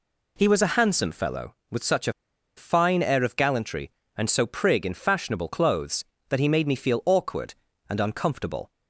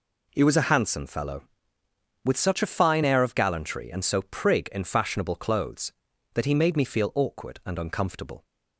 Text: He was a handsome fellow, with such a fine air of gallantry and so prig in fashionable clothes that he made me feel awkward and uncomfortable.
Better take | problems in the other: second | pauses between "a" and "fine"; at 2.1 s; 0.44 s long

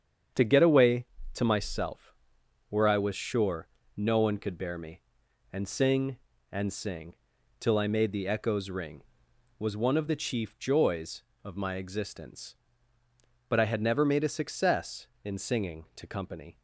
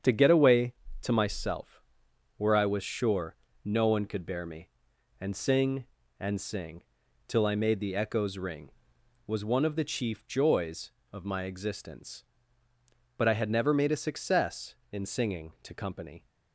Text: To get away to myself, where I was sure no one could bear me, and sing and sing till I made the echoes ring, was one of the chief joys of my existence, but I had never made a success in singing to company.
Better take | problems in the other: neither | starts louder than the rest; strong; the same in both // pauses between "sure" and "no"; slight; the same in both // pauses between "sing" and "till"; the same in both

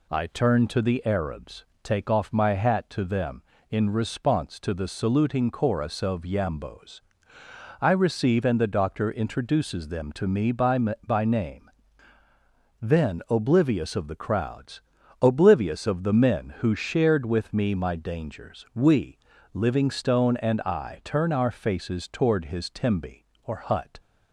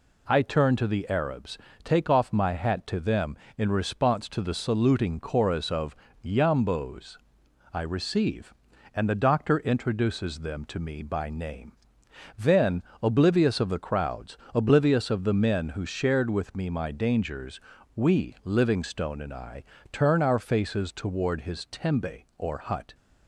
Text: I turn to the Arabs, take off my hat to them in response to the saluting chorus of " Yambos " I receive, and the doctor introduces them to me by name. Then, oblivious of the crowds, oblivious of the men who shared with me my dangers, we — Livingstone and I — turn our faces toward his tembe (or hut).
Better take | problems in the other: second | says "by" twice; at 10.7 s

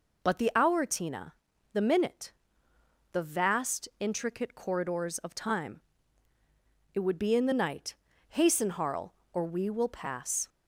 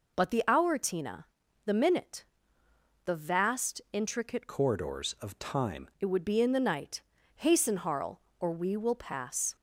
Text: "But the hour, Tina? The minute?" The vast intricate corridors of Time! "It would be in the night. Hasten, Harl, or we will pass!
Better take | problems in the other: first | changes voice from "corridors" to "Time"; from 4.4 to 5.8 s; 1.4 s long

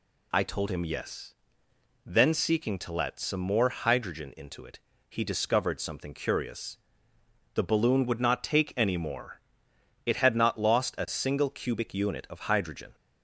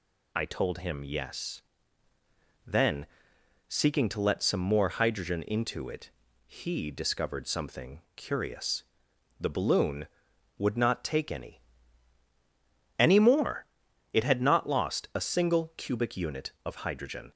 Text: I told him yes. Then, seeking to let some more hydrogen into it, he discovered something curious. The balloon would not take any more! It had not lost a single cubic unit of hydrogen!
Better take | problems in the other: first | pauses between "something" and "curious"; slight; at 8.0 s; 0.16 s long // says "any" twice; at 12.9 s

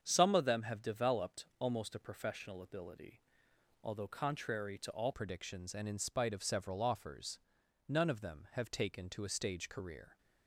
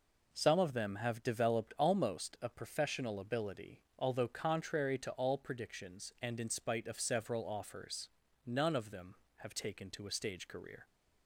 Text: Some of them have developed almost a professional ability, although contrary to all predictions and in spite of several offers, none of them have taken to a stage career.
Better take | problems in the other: second | starts louder than the rest; strong; until 1.0 s; 7.5 dB // changes voice at "predictions"; from 5.1 s on; 5.0 s long

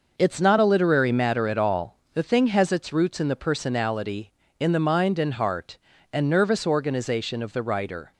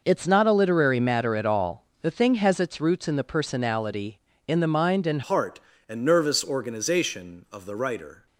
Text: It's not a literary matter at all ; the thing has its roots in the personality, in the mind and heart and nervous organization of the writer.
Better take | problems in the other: first | changes voice at "heart"; from 5.2 s on; 3.0 s long

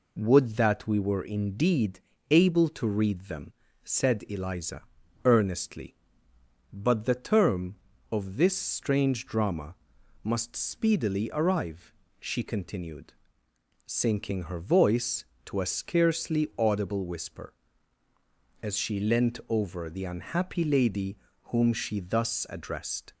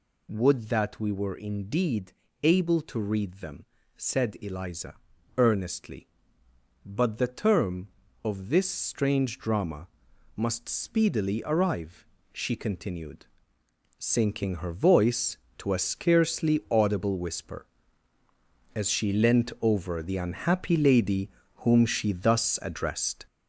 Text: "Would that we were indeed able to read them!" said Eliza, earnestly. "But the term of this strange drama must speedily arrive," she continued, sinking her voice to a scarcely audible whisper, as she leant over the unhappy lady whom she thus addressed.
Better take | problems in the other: first | gets louder; noticeable; throughout; 5.5 dB // pauses between "indeed" and "able"; slight; at 2.1 s; 0.32 s long; slight in the first // pauses between "drama" and "must"; noticeable; at 9.8 s; 0.48 s long; noticeable in the first // pauses between "lady" and "whom"; slight; at 21.2 s; 0.26 s long; slight in the first

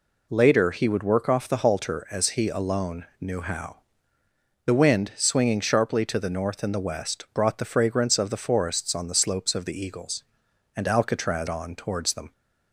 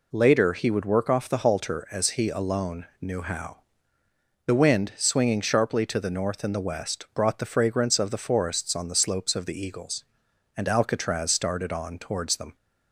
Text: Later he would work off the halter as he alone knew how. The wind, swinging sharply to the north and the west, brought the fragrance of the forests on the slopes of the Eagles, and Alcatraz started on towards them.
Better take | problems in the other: second | skips "started"; at 11.4 s

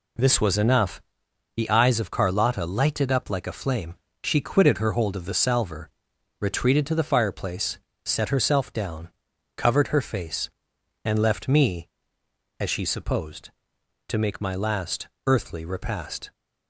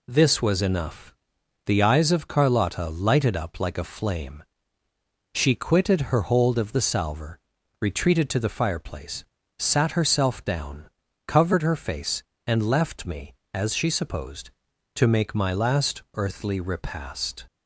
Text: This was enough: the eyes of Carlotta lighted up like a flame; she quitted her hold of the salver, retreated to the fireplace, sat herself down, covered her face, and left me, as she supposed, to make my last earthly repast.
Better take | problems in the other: second | says "set" for "sat"; at 8.0 s // pauses between "last" and "earthly"; slight; at 15.0 s; 0.20 s long

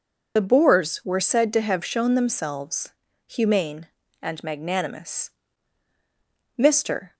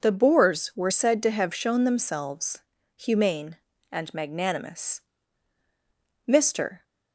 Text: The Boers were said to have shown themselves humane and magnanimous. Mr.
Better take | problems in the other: second | loses the start of "The"; at 0.3 s; 40 ms // pauses between "themselves" and "humane"; slight; at 2.9 s; 0.34 s long; slight in the second

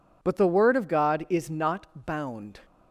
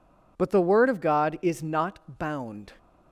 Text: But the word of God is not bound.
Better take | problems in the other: neither | none

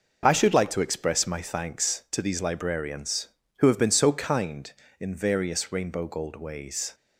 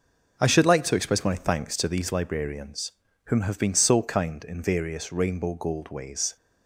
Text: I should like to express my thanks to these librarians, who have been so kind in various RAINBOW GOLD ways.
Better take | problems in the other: first | says "whom" for "who"; at 3.2 s

